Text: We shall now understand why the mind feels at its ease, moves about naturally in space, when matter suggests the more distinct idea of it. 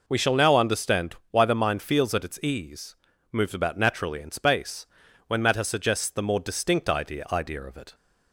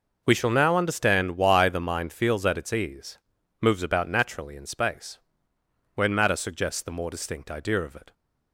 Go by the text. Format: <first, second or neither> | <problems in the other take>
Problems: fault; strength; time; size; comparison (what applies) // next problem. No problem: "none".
second | pauses between "understand" and "why"; slight; at 1.1 s; 0.16 s long // says "idea" twice; at 7.3 s